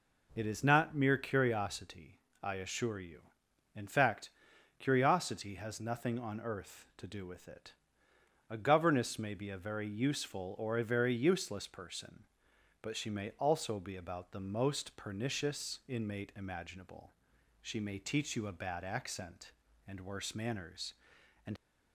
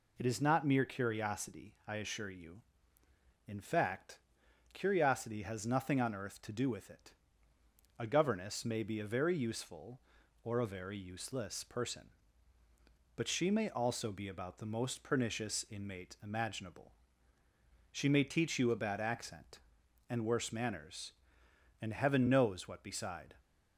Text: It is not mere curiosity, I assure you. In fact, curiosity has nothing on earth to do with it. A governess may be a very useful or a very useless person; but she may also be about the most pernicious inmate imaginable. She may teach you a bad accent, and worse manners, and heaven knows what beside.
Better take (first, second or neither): second